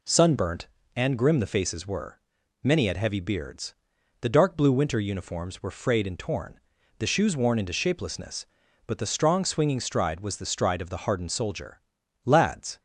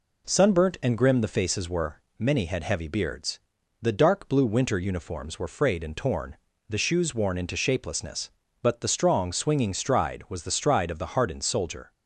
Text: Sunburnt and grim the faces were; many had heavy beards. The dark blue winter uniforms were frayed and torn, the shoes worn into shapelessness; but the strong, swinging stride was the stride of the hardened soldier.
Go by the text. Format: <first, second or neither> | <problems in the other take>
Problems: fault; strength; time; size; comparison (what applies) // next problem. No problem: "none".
second | goes on to say "Lads"; from 12.2 s on; 0.54 s long